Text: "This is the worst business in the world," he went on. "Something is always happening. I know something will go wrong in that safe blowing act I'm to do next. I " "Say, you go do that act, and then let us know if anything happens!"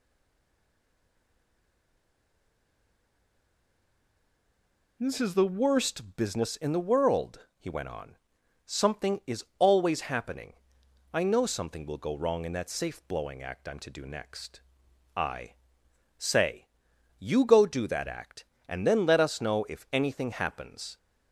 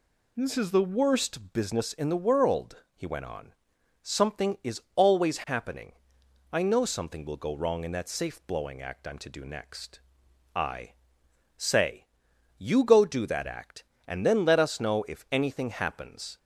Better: second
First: stays silent before the first word; strong; until 5.0 s; 5.0 s long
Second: none

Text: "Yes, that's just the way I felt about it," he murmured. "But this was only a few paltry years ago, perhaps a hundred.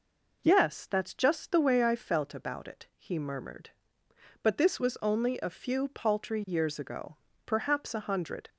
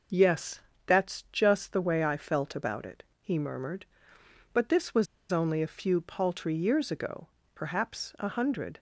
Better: first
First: none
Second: starts louder than the rest; until 1.4 s; 6.5 dB // pauses between "was" and "only"; slight; at 5.0 s; 0.24 s long

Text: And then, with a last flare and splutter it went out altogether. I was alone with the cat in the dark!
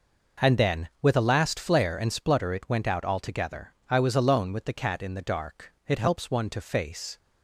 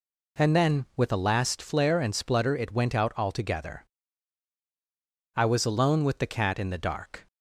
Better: second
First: goes on to say "It helps one to face"; noticeable; from 5.8 s on; 1.3 s long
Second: none

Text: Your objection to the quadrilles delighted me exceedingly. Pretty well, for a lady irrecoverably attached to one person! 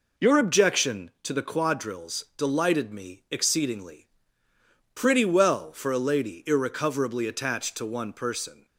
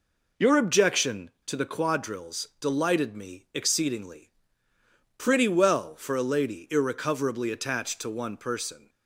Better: neither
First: none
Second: none

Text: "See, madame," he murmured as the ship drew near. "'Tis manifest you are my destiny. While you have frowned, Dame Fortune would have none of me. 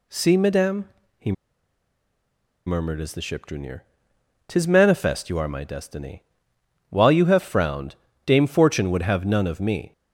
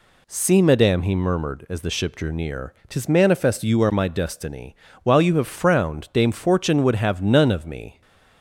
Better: second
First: pauses between "he" and "murmured"; strong; at 1.3 s; 1.3 s long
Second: none

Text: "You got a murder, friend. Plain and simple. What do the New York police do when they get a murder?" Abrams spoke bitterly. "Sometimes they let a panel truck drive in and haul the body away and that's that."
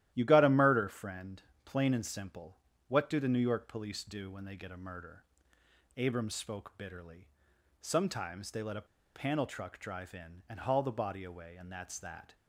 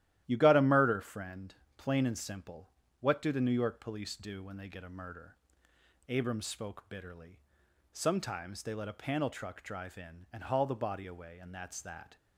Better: second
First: starts louder than the rest; strong; until 1.1 s; 13 dB // pauses between "a" and "panel"; slight; at 8.8 s; 0.29 s long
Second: starts louder than the rest; strong; until 1.2 s; 13 dB

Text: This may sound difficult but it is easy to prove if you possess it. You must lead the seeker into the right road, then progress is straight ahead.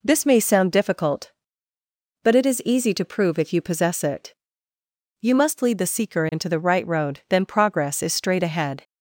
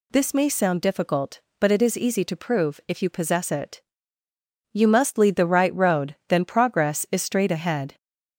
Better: first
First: none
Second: skips "the seeker into"; at 5.3 s

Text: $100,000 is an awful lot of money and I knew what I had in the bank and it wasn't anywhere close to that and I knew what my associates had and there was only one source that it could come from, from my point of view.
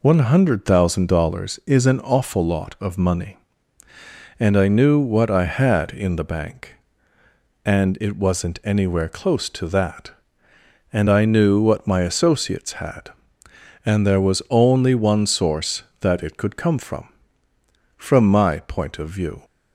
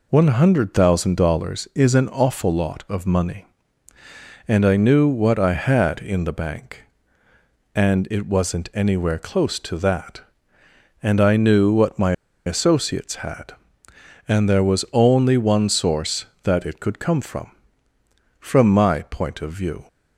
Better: first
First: none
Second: pauses between "my" and "associates"; slight; at 12.1 s; 0.33 s long

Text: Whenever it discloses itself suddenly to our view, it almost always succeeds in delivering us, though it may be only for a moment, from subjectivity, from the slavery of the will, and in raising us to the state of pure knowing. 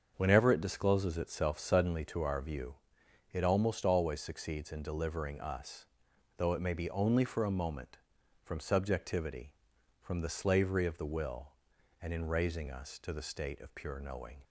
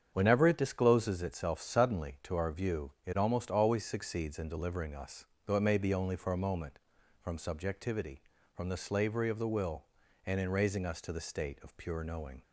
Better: neither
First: starts louder than the rest; until 1.1 s; 7 dB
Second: starts louder than the rest; strong; until 1.1 s; 8 dB

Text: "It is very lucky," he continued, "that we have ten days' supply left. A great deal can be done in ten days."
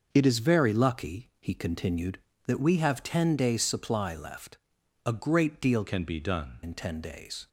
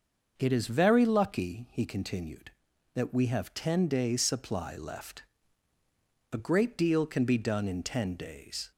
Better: second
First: starts louder than the rest; until 1.1 s; 6 dB // changes voice from "can" to "done"; from 5.8 to 6.6 s; 0.8 s long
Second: starts louder than the rest; until 1.3 s; 6 dB

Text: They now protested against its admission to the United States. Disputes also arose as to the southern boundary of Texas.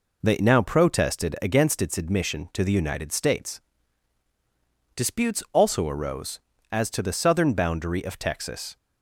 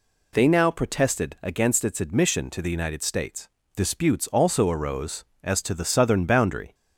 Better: first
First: none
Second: stops before "of Texas"; at 6.7 s

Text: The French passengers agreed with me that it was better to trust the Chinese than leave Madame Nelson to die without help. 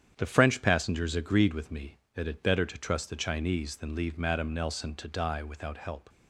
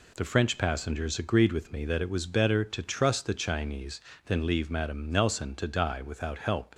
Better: second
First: starts louder than the rest; strong; until 1.1 s; 9 dB // skips "was"; at 2.4 s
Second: none

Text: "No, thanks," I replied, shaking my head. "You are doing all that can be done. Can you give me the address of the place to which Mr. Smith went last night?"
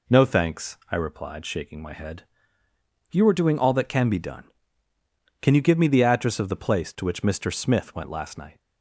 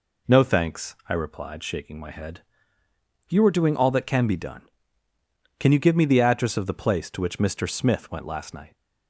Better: neither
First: none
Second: none

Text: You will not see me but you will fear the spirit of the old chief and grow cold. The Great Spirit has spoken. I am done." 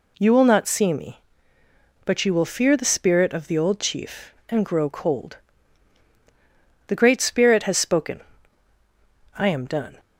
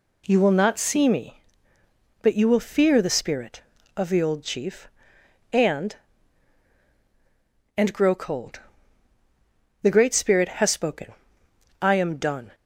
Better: first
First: none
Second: says "and" twice; at 7.7 s

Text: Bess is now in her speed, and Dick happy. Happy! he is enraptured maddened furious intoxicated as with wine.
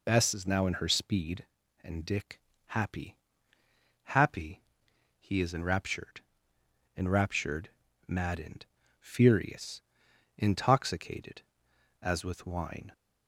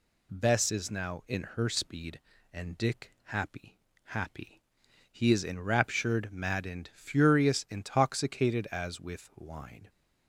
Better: second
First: pauses between "Dick" and "happy"; slight; at 2.4 s; 0.26 s long // says "enraptured" twice; at 6.9 s // pauses between "maddened" and "furious"; slight; at 8.6 s; 0.32 s long // pauses between "furious" and "intoxicated"; noticeable; at 9.8 s; 0.56 s long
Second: none

